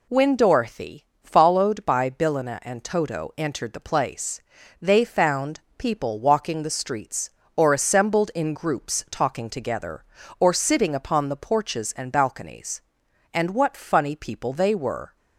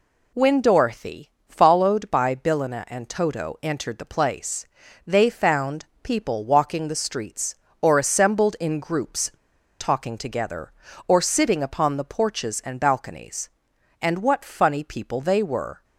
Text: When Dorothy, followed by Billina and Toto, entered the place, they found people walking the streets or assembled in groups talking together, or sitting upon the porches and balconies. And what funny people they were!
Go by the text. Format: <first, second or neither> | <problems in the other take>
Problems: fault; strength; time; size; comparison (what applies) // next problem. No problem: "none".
first | pauses between "found" and "people"; slight; at 5.8 s; 0.16 s long; slight in the first // pauses between "groups" and "talking"; noticeable; at 9.3 s; 0.48 s long